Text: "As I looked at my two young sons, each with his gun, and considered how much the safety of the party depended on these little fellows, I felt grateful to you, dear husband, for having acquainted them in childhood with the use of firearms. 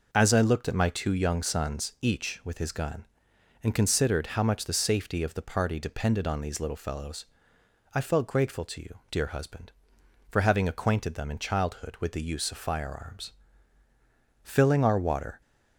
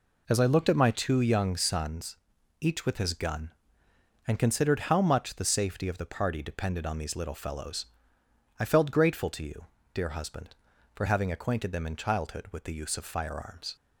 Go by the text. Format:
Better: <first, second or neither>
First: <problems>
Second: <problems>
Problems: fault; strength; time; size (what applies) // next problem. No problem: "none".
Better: second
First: goes on to say "Filling our water"; noticeable; from 14.4 s on; 0.98 s long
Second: none